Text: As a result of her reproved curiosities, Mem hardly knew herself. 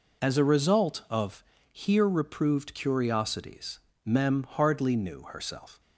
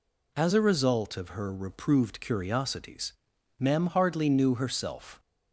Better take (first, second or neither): second